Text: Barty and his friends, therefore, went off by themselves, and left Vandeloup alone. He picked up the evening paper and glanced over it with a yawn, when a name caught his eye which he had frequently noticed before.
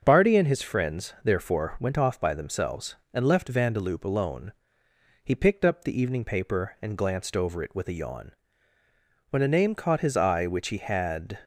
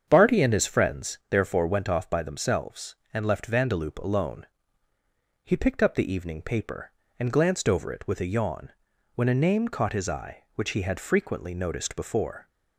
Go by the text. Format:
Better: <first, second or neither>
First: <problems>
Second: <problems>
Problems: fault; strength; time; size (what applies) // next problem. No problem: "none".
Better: second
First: starts louder than the rest; until 1.0 s; 7 dB // stops before "frequently noticed before"; at 11.4 s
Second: starts louder than the rest; strong; until 1.0 s; 7.5 dB